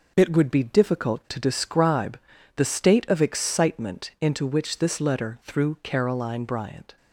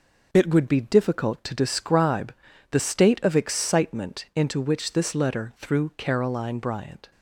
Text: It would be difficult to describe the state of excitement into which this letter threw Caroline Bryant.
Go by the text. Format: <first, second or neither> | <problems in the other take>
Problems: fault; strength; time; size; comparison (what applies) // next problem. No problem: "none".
neither | pauses between "describe" and "the"; the same in both